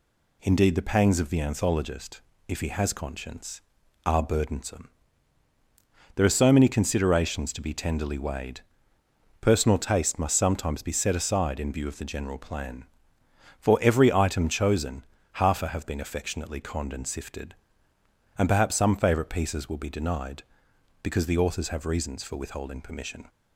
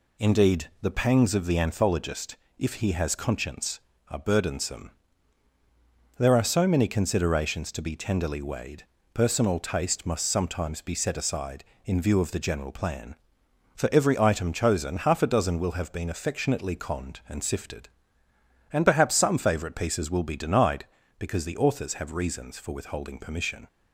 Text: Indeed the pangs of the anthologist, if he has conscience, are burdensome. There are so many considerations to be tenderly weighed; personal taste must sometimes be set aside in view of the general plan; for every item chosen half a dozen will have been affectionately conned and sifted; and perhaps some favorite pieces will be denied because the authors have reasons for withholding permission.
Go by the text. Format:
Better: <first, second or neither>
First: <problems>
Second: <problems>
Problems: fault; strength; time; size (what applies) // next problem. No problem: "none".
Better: second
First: pauses between "chosen" and "half"; slight; at 15.0 s; 0.30 s long // skips "dozen will"; at 15.6 s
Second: none